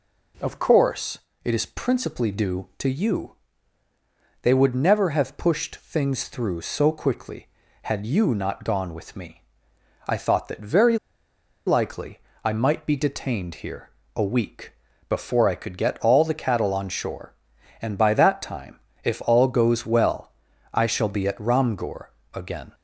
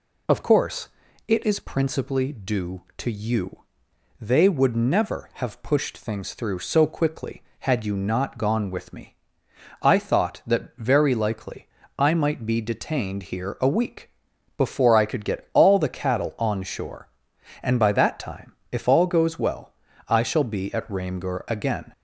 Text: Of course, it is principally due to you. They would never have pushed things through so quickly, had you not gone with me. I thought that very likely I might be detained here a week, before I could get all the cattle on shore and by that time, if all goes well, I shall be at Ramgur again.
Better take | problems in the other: second | pauses between "very" and "likely"; noticeable; at 10.9 s; 0.68 s long // pauses between "likely" and "I"; slight; at 12.1 s; 0.24 s long; slight in the second // pauses between "here" and "a"; slight; at 13.8 s; 0.26 s long // pauses between "Ramgur" and "again"; slight; at 22.0 s; 0.26 s long

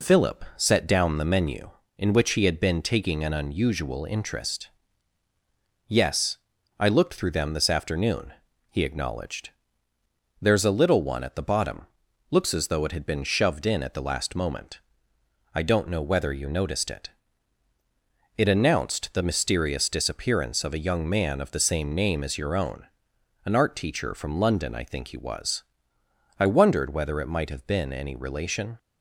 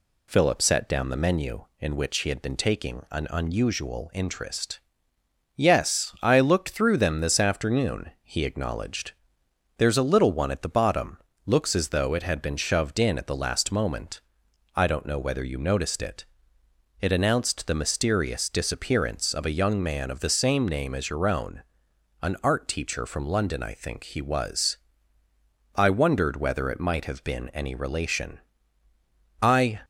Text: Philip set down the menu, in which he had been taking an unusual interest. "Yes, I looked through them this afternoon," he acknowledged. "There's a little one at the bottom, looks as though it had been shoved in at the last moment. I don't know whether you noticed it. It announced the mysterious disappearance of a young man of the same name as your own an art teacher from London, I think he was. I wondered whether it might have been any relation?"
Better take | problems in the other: first | pauses between "own" and "an"; noticeable; at 21.6 s; 0.58 s long; noticeable in the first // goes on to say "I"; slight; from 29.4 s on; 0.40 s long

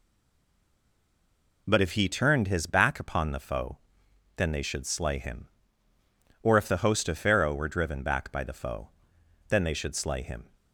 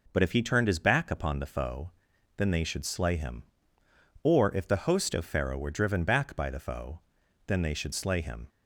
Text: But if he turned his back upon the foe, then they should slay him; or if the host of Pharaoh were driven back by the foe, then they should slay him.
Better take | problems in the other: second | stays silent before the first word; noticeable; until 1.6 s; 1.6 s long

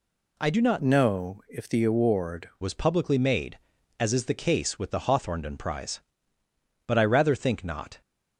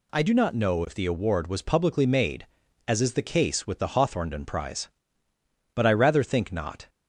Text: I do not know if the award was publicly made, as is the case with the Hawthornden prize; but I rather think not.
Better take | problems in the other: second | changes voice from "know" to "award"; from 0.7 to 2.4 s; 1.7 s long

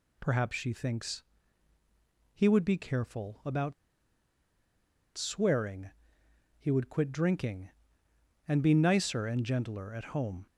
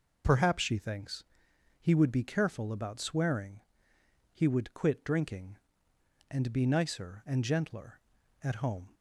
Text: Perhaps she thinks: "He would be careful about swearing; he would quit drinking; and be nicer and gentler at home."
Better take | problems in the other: second | pauses between "about" and "swearing"; strong; at 3.7 s; 1.4 s long

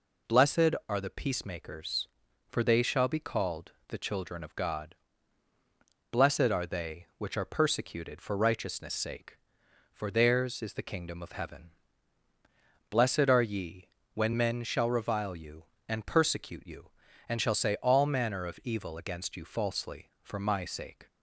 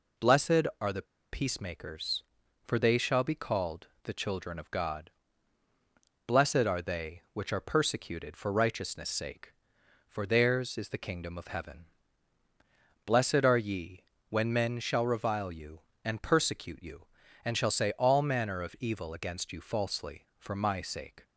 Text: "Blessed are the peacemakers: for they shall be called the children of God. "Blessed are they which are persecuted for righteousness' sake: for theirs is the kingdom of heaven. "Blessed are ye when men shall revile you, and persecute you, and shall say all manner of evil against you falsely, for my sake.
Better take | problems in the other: first | pauses between "the" and "peacemakers"; slight; at 1.0 s; 0.26 s long // pauses between "called" and "the"; slight; at 3.8 s; 0.16 s long; slight in the first // pauses between "ye" and "when"; slight; at 14.0 s; 0.26 s long; slight in the first

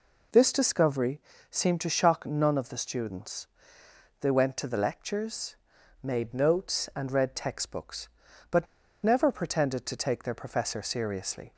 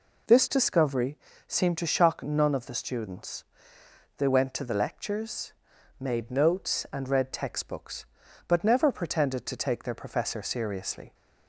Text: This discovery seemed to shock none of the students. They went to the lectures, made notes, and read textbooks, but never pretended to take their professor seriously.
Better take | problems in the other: second | pauses between "discovery" and "seemed"; slight; at 1.2 s; 0.30 s long; slight in the second // pauses between "but" and "never"; at 8.6 s; 0.37 s long

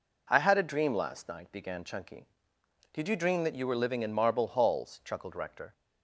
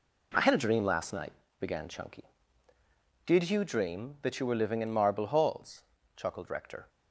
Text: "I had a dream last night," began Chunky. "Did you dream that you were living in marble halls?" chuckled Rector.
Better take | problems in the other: first | gets quieter; strong; throughout; 9.5 dB

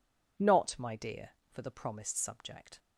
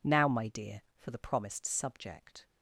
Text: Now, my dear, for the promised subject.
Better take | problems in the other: second | says "Not" for "Now"; at 0.3 s

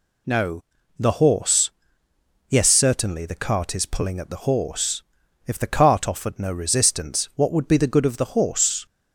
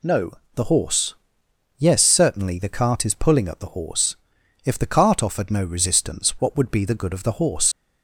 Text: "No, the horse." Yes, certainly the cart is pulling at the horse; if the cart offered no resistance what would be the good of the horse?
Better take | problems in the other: first | leaves "horse" unfinished; at 7.7 s; 80 ms

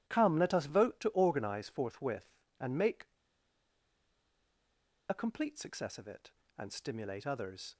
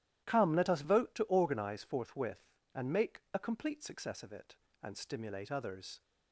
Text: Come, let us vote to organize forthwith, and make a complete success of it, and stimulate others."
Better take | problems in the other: second | starts louder than the rest; strong; until 1.0 s; 13 dB; strong in the second // pauses between "make" and "a"; strong; at 3.0 s; 2.0 s long

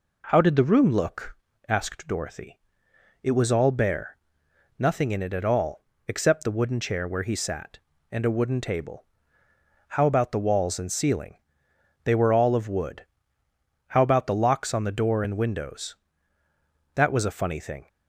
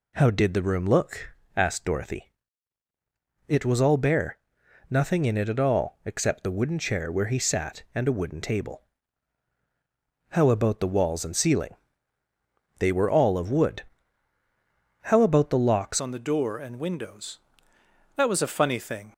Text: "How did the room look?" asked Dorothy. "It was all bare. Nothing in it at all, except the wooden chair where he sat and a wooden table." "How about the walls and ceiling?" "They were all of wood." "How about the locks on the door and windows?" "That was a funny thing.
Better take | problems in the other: first | changes voice at "on"; from 15.9 s on; 3.2 s long

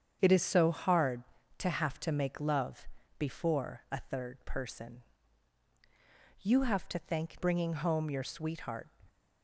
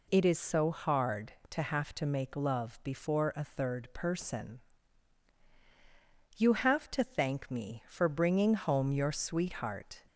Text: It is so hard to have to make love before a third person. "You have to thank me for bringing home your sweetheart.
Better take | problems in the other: second | starts louder than the rest; strong; until 1.2 s; 8 dB // pauses between "love" and "before"; slight; at 2.8 s; 0.30 s long // skips "me for"; at 7.4 s

